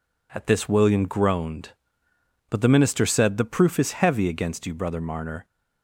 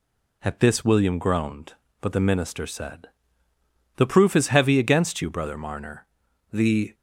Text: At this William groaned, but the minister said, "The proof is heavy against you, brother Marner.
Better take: first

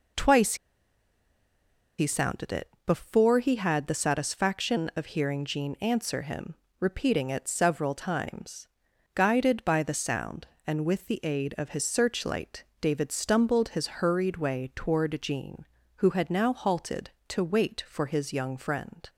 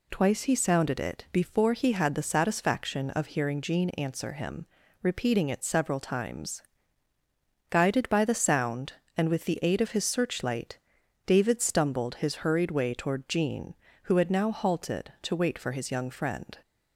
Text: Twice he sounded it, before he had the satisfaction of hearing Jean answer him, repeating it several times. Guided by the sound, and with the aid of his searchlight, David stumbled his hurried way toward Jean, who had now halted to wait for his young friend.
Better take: second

